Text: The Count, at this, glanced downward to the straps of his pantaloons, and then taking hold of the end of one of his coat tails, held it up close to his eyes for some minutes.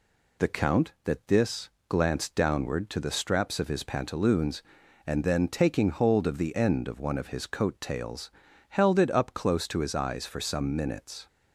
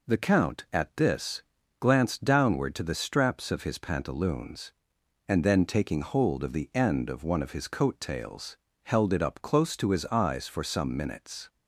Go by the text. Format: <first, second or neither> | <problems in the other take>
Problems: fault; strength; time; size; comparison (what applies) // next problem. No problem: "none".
second | says "that" for "at"; at 1.0 s